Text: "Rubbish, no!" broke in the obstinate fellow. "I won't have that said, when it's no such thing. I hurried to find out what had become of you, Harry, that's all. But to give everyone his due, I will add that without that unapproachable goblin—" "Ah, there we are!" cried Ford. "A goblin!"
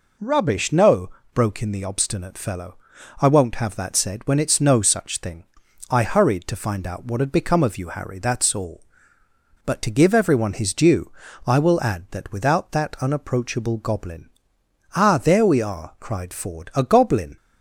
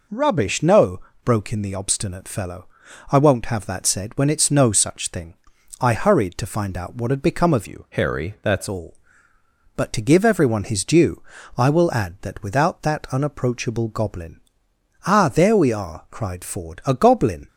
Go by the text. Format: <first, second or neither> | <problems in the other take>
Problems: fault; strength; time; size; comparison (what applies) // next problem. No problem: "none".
first | changes voice from "you" to "that's"; from 7.6 to 8.6 s; 1.0 s long